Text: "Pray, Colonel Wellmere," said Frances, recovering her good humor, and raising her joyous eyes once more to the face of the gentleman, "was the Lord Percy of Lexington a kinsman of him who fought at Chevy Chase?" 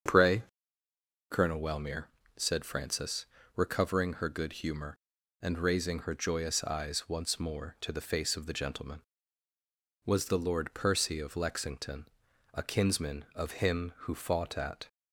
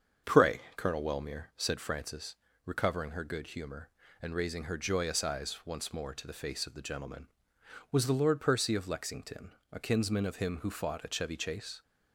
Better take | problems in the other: second | starts louder than the rest; until 1.9 s; 7 dB; also in the second // pauses between "Lexington" and "a"; noticeable; at 12.0 s; 0.46 s long; slight in the second // stops before "Chevy Chase"; at 14.8 s

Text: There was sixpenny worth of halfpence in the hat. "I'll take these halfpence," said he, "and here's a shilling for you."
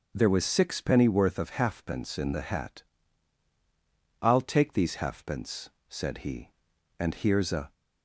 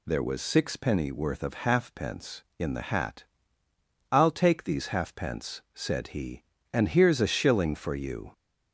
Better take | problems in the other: second | stops before "shilling for you"; at 7.7 s

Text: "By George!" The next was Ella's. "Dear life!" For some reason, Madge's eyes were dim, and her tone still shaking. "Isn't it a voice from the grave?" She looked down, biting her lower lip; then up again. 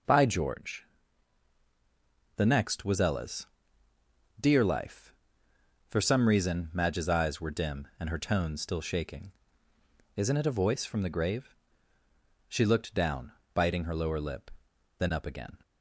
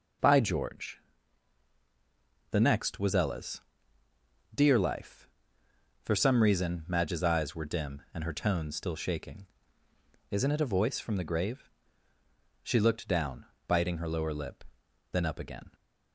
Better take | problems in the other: neither | none

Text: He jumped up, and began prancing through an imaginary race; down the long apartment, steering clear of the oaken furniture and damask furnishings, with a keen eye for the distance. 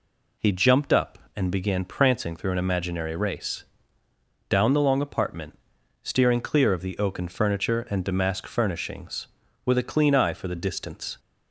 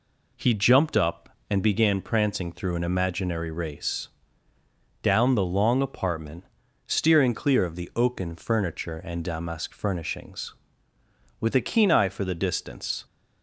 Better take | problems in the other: second | says "clean" for "keen"; at 9.8 s

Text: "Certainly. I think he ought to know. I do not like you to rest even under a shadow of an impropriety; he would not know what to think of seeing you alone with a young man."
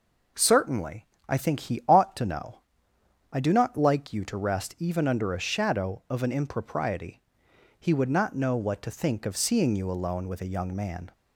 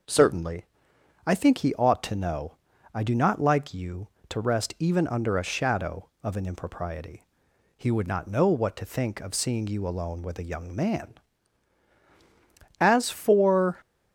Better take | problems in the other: first | goes on to say "As for"; noticeable; from 12.7 s on; 1.0 s long

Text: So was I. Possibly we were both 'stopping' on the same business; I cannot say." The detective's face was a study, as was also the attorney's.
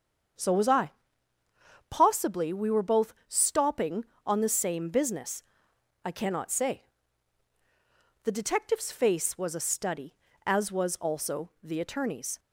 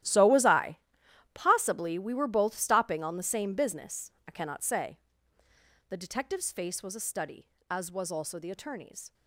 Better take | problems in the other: first | gets quieter; strong; throughout; 16 dB // starts louder than the rest; strong; until 1.6 s; 13 dB; strong in the first

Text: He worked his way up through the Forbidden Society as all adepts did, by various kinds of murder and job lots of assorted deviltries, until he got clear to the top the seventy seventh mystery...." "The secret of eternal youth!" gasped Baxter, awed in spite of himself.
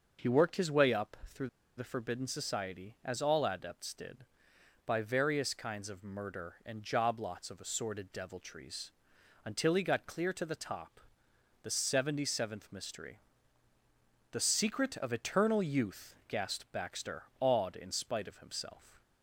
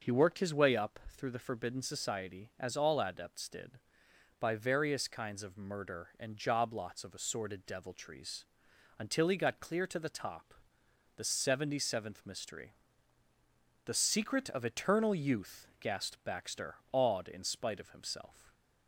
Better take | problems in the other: second | pauses between "up" and "through"; slight; at 1.1 s; 0.18 s long; slight in the second // pauses between "through" and "the"; slight; at 1.4 s; 0.29 s long // pauses between "top" and "the"; noticeable; at 11.0 s; 0.62 s long; noticeable in the second

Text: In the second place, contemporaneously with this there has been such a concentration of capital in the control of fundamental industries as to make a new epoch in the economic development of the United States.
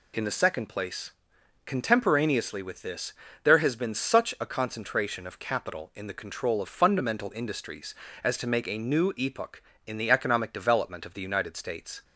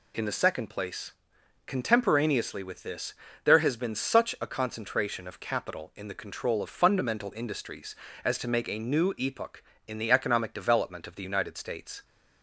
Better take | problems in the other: neither | pauses between "this" and "there"; slight; the same in both

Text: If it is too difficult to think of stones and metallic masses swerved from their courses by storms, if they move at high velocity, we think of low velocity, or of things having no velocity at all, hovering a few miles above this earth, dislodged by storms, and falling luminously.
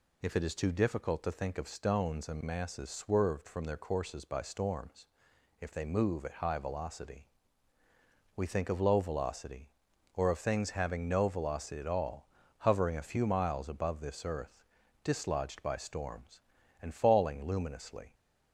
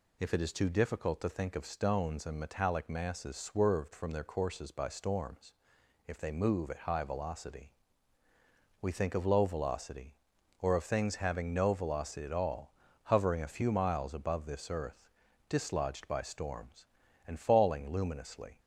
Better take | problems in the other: second | skips "metallic"; at 2.4 s

